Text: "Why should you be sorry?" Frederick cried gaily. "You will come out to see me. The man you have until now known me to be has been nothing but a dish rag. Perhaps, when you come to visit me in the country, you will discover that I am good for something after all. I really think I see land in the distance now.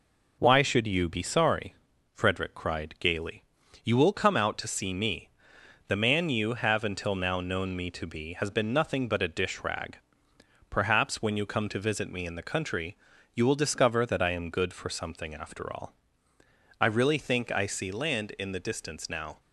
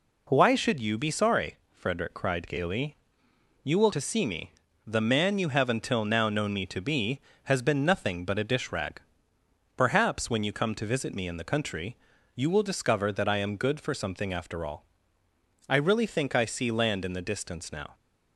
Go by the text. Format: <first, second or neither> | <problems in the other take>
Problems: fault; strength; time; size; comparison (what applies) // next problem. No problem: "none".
first | skips "come out"; at 3.9 s